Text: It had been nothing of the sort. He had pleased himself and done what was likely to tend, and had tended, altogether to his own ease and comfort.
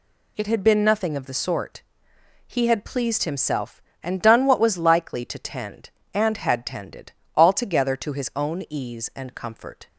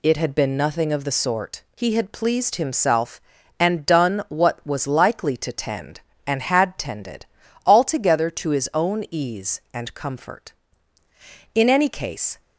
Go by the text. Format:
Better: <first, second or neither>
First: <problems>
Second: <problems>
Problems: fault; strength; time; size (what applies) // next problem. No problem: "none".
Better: first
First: none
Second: goes on to say "In any case"; noticeable; from 11.5 s on; 0.86 s long